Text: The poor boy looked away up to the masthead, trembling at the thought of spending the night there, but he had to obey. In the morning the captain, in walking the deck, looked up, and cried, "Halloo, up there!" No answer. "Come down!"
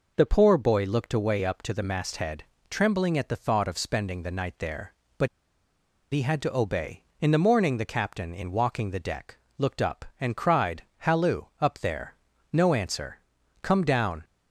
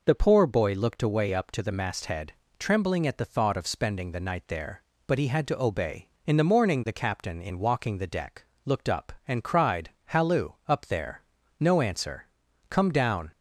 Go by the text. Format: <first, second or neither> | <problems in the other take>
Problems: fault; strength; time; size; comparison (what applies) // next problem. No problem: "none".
second | pauses between "but" and "he"; noticeable; at 5.2 s; 0.85 s long